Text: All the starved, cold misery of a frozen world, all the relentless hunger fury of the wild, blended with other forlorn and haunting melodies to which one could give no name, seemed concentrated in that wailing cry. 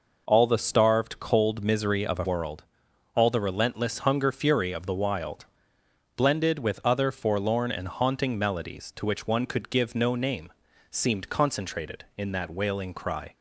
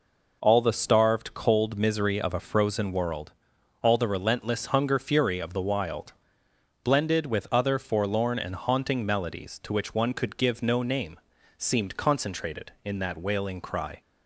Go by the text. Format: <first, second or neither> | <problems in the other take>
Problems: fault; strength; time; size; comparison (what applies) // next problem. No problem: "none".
second | skips "frozen"; at 2.2 s